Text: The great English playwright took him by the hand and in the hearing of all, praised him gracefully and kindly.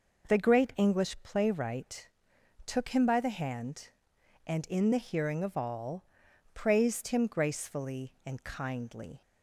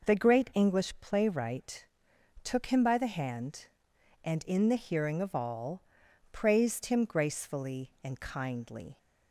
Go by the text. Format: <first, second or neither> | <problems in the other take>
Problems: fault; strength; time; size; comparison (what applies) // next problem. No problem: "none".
neither | pauses between "playwright" and "took"; noticeable; the same in both